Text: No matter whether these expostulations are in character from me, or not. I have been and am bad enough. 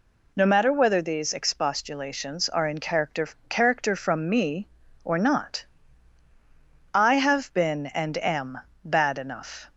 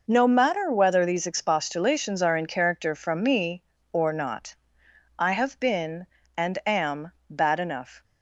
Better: second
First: says "character" twice; at 3.4 s // pauses between "am" and "bad"; slight; at 8.5 s; 0.24 s long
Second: pauses between "am" and "bad"; slight; at 7.1 s; 0.16 s long

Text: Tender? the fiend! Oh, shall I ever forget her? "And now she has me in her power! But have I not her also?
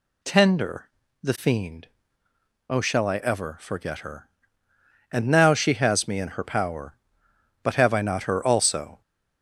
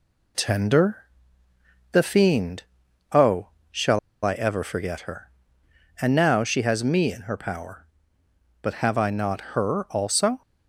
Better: first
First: none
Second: pauses between "shall" and "I"; slight; at 3.9 s; 0.26 s long

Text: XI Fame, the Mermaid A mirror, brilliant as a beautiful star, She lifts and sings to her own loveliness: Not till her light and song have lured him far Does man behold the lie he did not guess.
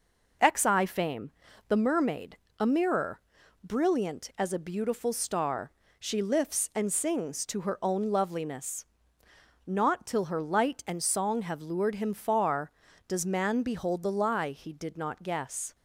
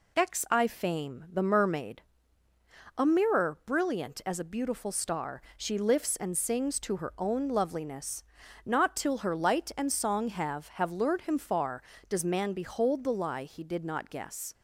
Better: first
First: pauses between "Mermaid" and "A"; slight; at 2.3 s; 0.22 s long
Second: pauses between "Mermaid" and "A"; noticeable; at 2.0 s; 0.96 s long // says "have" twice; at 10.6 s

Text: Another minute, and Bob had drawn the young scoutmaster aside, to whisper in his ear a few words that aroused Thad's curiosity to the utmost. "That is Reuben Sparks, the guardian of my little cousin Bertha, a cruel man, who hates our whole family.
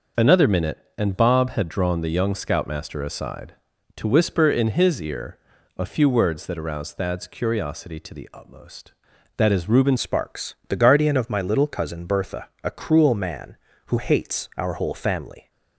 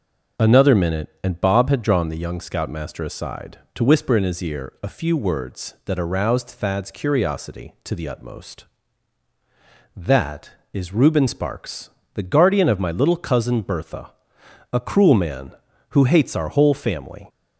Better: second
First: pauses between "ear" and "a"; at 5.3 s; 0.38 s long // changes voice at "Sparks"; from 9.9 s on; 5.6 s long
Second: none

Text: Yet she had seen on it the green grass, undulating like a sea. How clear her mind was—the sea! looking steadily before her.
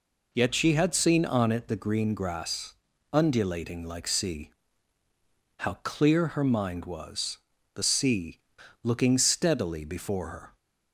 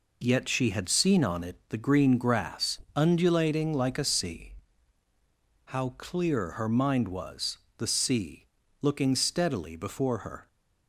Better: second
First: skips "a"; at 4.0 s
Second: none

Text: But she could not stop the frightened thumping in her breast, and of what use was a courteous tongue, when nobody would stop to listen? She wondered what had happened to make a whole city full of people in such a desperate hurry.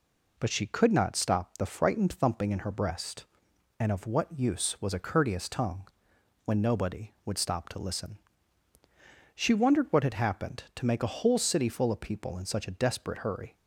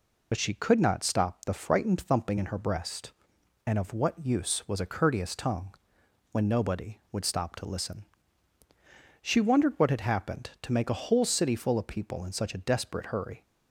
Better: first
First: none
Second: loses the start of "But"; at 0.3 s; 55 ms

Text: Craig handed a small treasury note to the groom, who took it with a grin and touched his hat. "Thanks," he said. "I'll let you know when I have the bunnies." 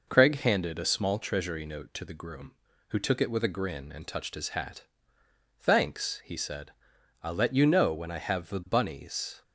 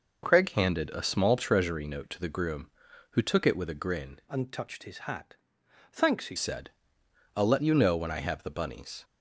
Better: first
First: none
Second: changes voice from "and" to "he"; from 4.2 to 6.3 s; 2.1 s long

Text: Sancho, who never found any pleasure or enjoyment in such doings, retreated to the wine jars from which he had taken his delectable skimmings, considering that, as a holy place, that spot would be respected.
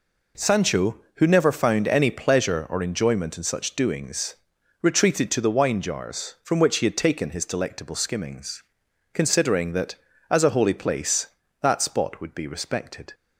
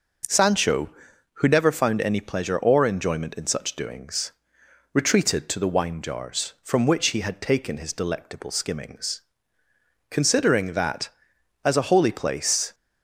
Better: first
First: none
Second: starts louder than the rest; noticeable; until 1.7 s; 6 dB // stops before "that spot would be respected"; at 12.7 s

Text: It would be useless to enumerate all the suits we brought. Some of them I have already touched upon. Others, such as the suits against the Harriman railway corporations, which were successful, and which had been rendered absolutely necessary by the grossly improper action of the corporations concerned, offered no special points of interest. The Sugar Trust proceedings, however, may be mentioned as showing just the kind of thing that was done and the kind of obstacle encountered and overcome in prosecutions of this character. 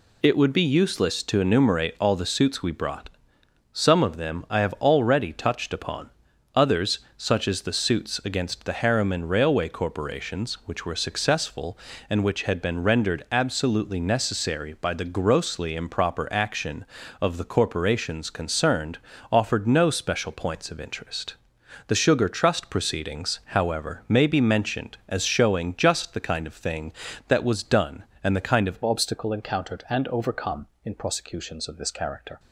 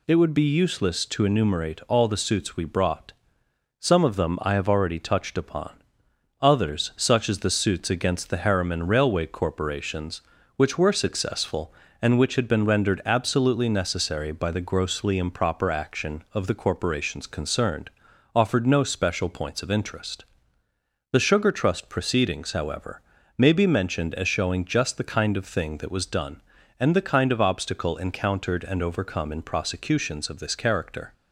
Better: second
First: changes voice at "obstacle"; from 28.8 s on; 3.5 s long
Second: none

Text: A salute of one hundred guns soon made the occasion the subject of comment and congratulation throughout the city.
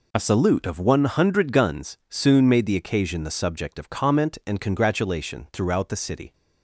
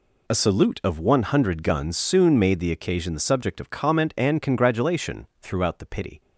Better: first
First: none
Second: says "pity" for "city"; at 5.8 s

